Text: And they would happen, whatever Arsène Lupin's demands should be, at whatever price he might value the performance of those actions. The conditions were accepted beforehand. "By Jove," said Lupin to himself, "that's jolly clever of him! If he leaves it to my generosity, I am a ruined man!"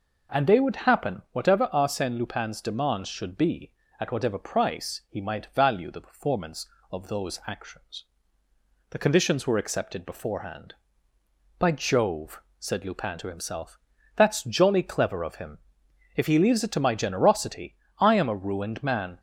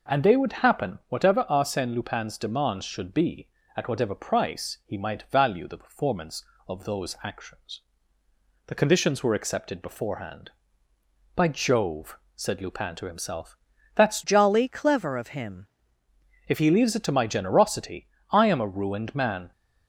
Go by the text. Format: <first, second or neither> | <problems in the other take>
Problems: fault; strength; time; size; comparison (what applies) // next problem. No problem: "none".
first | changes voice from "jolly" to "him"; from 14.2 to 15.6 s; 1.4 s long